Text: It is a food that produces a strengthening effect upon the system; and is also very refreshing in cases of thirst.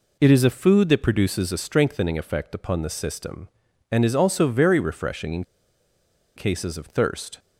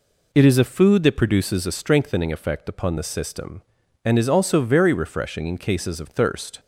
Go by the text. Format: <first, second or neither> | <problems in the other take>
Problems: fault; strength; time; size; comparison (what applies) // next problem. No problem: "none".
second | pauses between "in" and "cases"; noticeable; at 5.4 s; 0.92 s long